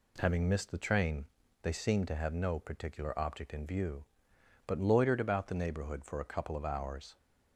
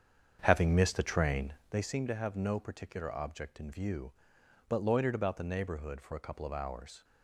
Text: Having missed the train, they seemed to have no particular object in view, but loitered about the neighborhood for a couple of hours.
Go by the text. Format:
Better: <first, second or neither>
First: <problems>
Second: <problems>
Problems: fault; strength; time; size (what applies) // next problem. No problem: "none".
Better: first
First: none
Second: starts louder than the rest; strong; until 1.9 s; 7.5 dB